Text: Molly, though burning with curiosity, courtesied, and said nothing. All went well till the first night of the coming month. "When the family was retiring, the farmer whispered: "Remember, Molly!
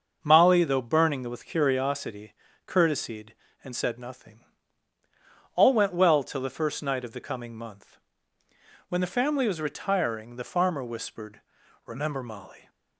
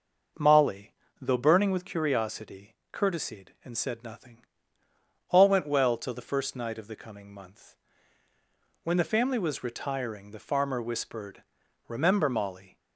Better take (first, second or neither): neither